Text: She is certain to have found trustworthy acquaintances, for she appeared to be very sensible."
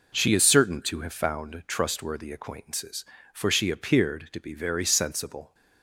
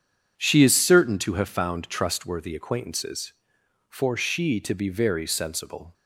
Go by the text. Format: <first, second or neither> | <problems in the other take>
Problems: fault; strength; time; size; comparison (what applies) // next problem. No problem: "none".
first | skips "appeared"; at 4.6 s